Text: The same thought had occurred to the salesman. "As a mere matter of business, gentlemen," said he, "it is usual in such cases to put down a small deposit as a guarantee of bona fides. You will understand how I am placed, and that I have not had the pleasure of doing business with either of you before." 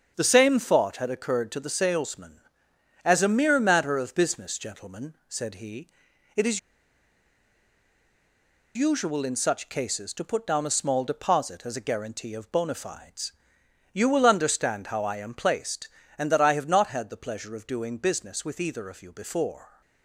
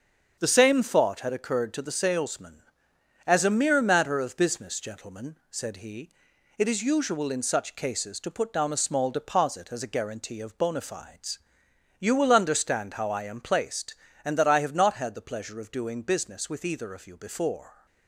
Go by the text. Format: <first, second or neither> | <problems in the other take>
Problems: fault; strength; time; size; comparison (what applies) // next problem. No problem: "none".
second | starts louder than the rest; until 1.1 s; 7 dB; also in the second // pauses between "is" and "usual"; strong; at 6.5 s; 2.1 s long